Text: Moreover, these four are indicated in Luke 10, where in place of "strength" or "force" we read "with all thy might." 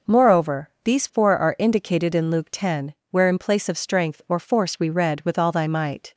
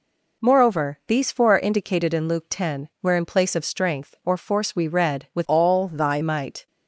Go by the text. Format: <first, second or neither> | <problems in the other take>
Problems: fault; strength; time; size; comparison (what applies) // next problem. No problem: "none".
first | changes voice from "all" to "thy"; from 5.4 to 6.1 s; 0.7 s long